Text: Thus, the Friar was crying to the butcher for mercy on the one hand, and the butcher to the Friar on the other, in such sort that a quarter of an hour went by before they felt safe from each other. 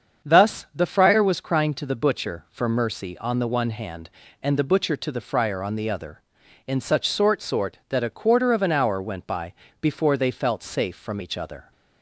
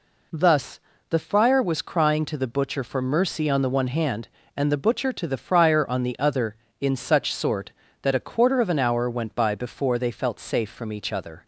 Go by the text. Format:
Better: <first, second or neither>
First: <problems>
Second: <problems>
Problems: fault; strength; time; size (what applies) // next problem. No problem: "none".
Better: second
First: starts louder than the rest; strong; until 1.3 s; 7 dB // says "sort" twice; at 7.4 s // pauses between "by" and "before"; slight; at 9.5 s; 0.26 s long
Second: none